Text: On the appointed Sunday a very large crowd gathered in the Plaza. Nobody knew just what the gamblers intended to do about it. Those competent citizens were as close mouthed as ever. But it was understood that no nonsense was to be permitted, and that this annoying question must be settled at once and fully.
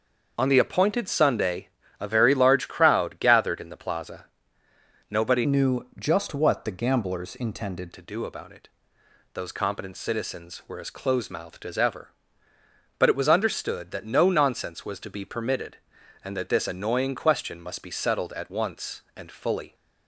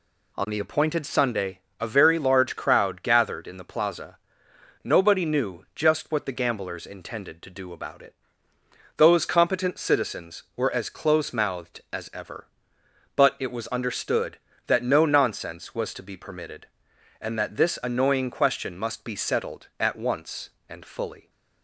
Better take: second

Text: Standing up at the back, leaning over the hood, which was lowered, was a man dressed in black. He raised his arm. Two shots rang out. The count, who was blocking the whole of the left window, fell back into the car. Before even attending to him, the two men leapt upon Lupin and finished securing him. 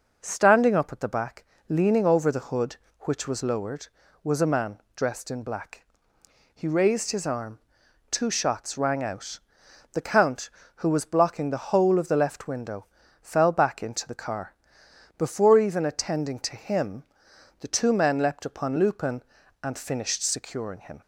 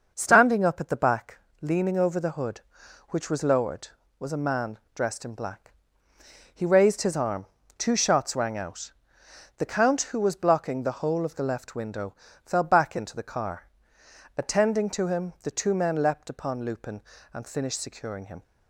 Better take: first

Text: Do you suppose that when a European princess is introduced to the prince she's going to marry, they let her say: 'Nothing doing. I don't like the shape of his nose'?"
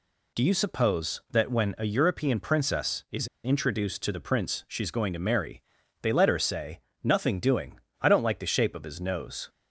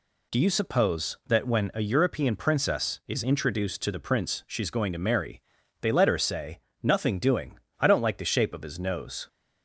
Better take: second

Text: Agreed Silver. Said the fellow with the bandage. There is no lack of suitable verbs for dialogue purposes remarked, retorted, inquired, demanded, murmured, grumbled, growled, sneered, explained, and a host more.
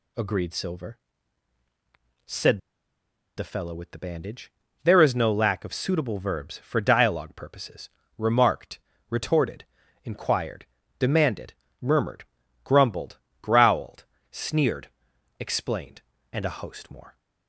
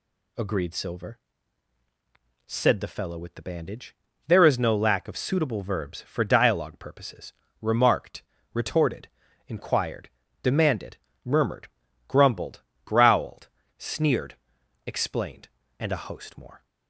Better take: second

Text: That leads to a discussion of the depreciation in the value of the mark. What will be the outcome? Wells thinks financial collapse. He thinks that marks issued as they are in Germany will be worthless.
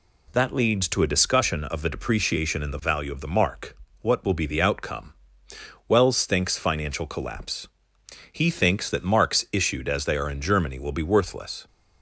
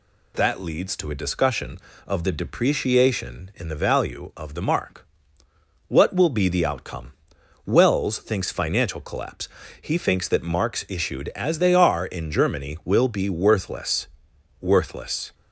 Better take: first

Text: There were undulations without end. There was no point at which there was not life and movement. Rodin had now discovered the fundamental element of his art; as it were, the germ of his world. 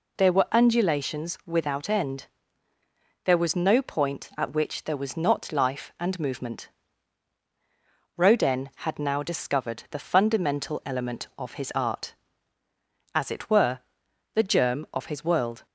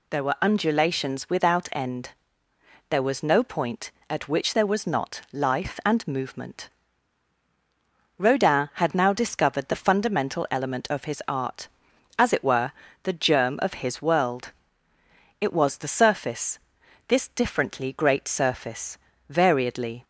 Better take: first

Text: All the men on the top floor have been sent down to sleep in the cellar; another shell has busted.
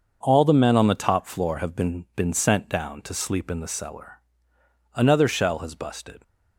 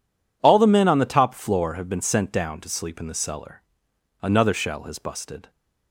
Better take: second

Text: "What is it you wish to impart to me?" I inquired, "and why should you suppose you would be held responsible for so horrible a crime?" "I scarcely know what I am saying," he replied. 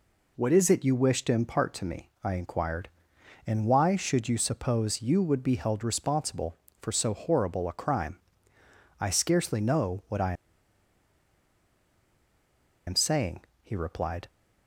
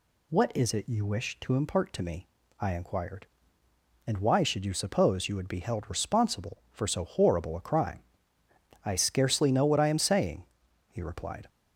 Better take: second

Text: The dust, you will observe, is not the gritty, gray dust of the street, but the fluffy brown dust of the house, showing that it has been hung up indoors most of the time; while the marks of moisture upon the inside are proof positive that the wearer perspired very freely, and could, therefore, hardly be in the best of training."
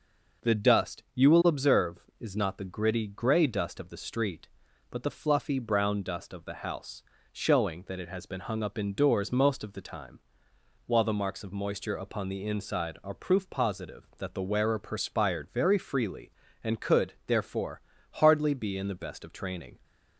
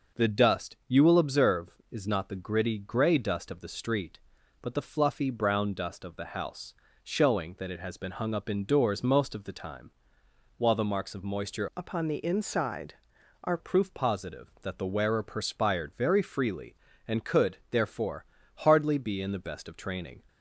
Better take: first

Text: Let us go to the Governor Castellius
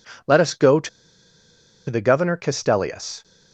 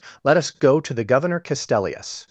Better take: second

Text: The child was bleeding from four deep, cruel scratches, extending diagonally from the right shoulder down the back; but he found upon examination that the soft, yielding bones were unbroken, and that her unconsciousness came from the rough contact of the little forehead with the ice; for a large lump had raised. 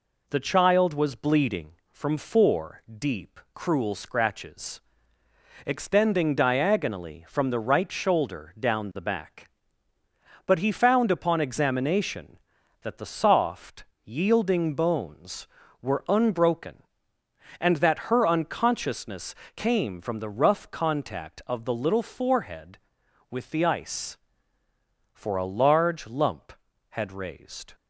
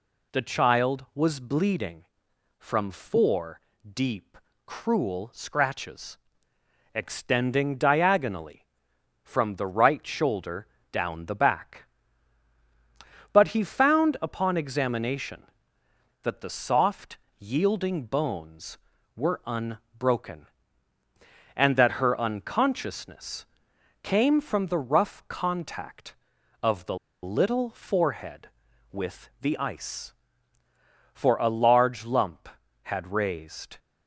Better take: first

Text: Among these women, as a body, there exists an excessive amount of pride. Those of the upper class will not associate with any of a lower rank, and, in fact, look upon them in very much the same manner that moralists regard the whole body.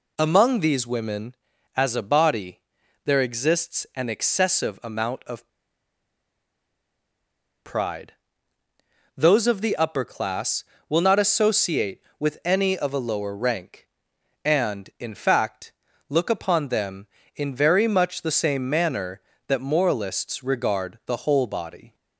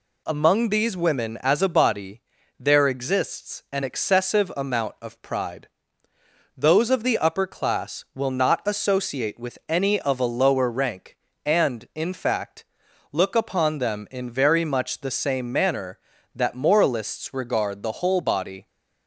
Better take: second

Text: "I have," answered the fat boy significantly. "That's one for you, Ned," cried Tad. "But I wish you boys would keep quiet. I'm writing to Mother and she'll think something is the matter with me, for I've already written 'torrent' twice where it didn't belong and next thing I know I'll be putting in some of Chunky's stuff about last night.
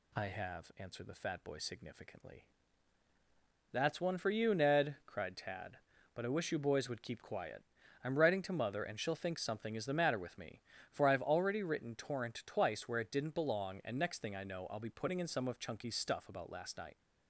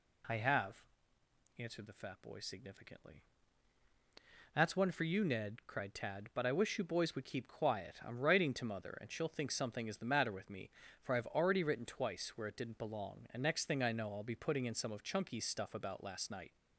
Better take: first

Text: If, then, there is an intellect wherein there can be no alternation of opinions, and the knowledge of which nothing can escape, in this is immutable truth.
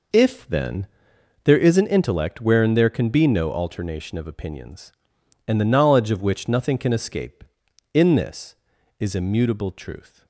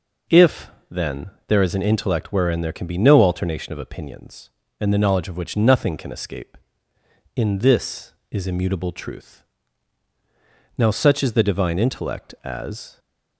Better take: first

